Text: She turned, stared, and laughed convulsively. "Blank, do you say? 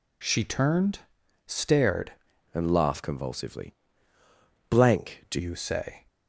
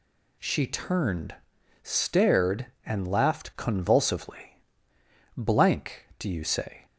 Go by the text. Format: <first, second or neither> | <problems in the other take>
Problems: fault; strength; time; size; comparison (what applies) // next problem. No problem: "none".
second | changes voice from "and" to "do"; from 2.5 to 5.3 s; 2.8 s long